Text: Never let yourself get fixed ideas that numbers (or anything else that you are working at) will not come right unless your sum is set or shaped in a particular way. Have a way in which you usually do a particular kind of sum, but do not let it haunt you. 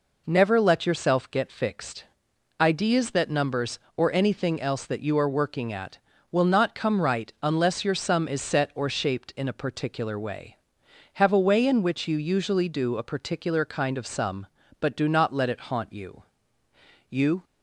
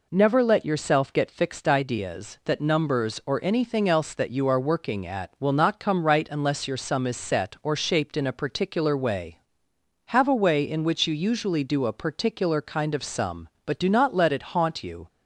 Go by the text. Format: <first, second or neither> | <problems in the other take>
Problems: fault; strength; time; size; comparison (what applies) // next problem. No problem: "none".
second | pauses between "fixed" and "ideas"; noticeable; at 2.0 s; 0.52 s long // goes on to say "You"; slight; from 17.0 s on; 0.34 s long